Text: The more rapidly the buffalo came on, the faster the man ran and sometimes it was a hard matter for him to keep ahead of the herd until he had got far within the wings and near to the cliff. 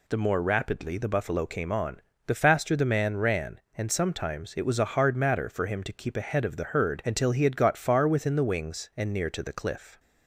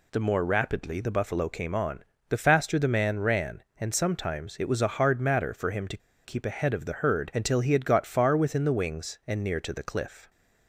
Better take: first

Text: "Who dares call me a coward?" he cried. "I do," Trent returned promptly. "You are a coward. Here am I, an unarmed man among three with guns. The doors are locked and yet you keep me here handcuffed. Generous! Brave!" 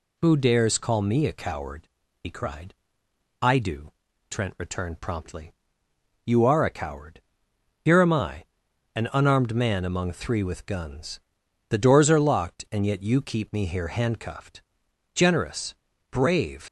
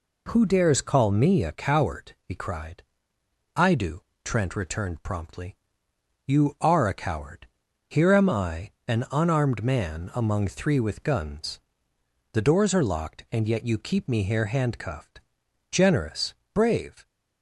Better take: second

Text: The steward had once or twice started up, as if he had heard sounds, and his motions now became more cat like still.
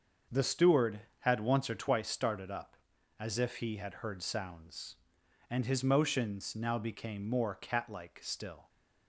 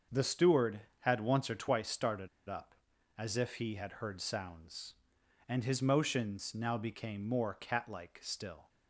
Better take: first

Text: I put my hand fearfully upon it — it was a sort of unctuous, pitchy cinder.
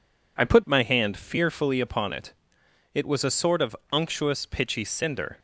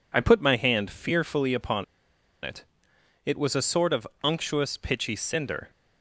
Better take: first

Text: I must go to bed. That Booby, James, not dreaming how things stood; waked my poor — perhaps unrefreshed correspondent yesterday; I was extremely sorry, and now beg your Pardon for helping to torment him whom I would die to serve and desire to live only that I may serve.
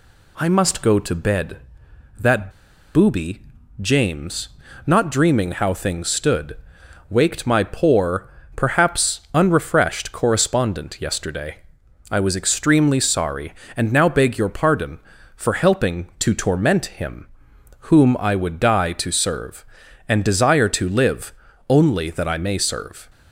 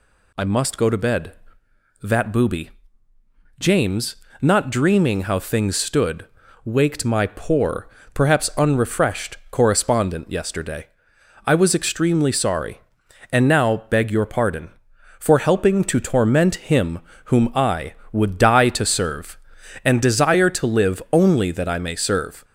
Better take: second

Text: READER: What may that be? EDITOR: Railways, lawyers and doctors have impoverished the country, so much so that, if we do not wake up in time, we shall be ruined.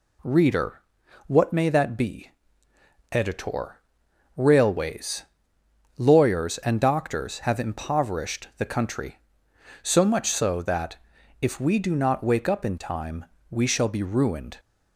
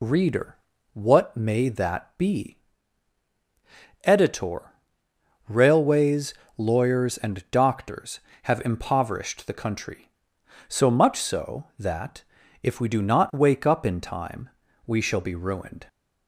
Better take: first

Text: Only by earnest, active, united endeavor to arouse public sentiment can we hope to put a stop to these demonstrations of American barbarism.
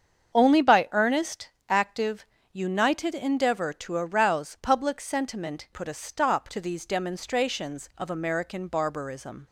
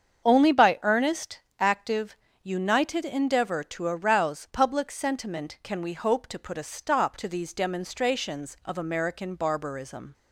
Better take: second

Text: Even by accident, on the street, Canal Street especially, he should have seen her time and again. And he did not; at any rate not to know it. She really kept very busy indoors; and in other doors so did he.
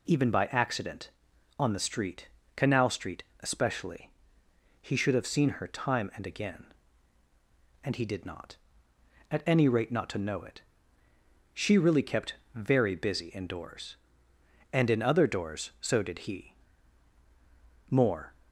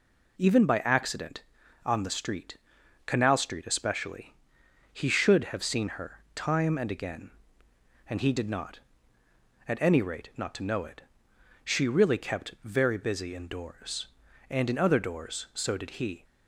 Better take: second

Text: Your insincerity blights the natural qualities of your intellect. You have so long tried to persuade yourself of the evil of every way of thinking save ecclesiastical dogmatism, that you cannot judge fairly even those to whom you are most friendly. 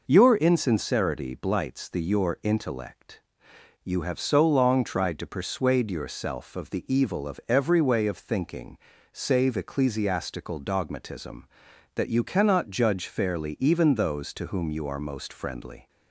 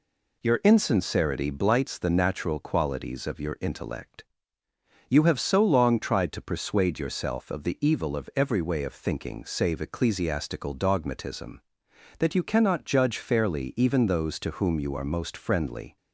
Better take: second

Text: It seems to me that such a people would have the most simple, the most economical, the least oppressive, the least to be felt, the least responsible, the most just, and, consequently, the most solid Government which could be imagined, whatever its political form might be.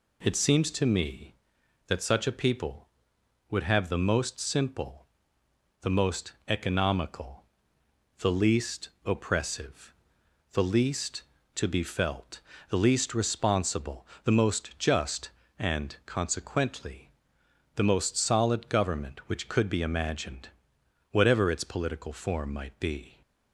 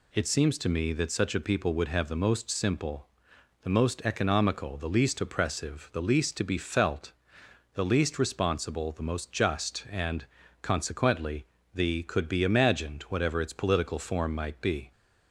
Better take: first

